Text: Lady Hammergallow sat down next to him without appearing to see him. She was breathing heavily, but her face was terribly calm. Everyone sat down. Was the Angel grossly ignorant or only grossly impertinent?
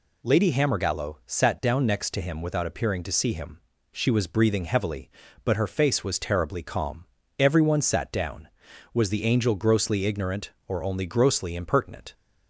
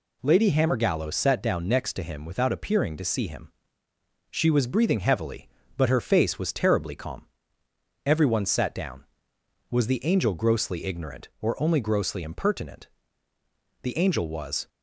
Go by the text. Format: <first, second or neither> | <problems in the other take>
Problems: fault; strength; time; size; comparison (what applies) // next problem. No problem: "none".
first | goes on to say "The Angel was"; noticeable; from 13.8 s on; 0.86 s long